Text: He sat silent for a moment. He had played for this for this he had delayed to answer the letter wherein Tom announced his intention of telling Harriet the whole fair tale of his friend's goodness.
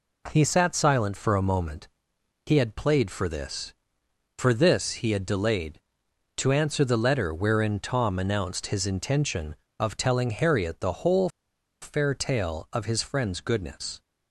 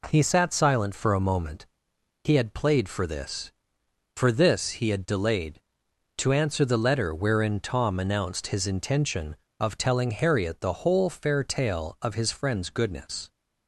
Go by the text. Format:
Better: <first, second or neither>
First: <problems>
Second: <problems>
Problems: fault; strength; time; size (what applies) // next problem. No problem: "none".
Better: second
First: pauses between "whole" and "fair"; noticeable; at 11.2 s; 0.54 s long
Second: none